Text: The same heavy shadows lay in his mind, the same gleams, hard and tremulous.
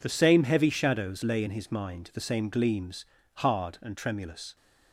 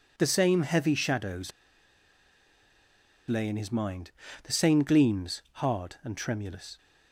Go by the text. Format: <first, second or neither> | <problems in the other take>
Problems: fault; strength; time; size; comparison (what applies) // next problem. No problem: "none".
first | pauses between "shadows" and "lay"; strong; at 1.4 s; 1.7 s long